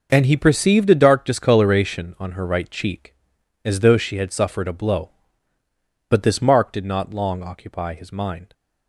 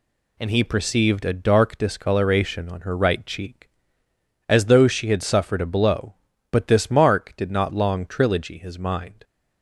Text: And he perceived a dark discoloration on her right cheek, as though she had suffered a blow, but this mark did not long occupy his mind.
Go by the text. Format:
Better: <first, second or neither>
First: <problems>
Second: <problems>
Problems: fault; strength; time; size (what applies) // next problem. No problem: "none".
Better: first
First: none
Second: says "trilogy" for "occupy"; at 8.0 s